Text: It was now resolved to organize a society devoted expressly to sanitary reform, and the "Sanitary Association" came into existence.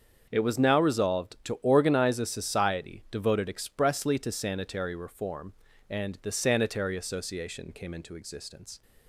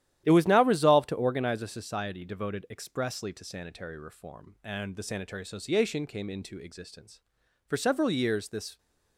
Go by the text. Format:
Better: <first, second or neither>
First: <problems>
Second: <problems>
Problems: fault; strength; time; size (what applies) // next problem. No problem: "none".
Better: first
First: starts louder than the rest; until 1.3 s; 7 dB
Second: starts louder than the rest; strong; until 1.2 s; 12 dB // goes on to say "For several years this"; noticeable; from 7.6 s on; 1.1 s long